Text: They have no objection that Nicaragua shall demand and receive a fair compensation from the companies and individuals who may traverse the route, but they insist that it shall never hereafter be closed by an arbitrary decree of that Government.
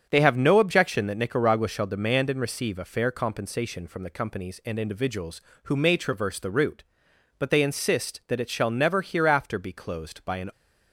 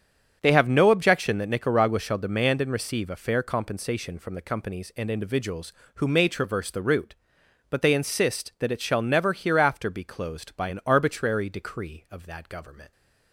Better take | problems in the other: second | starts louder than the rest; strong; until 1.1 s; 7.5 dB; strong in the second // stops before "arbitrary decree of that Government"; at 10.5 s

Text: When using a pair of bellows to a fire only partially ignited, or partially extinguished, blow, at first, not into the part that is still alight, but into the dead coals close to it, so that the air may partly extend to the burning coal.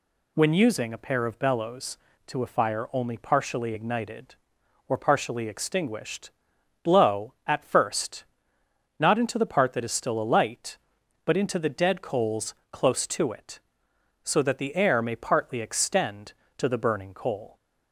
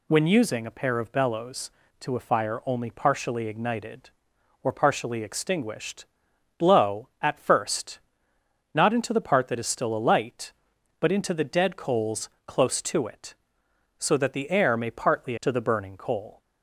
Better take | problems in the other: first | pauses between "coals" and "close"; slight; at 12.2 s; 0.16 s long; slight in the first // skips "extend"; at 15.3 s

